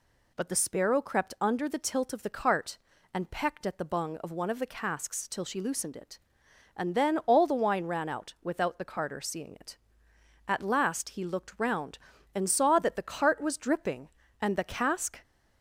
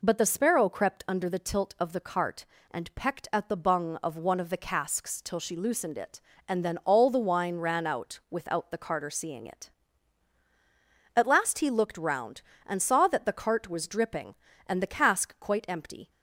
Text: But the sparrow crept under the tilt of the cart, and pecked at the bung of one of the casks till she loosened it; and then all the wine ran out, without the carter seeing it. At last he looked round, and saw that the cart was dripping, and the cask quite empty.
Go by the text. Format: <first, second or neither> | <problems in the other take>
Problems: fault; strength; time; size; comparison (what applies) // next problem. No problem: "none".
second | stops before "quite empty"; at 15.2 s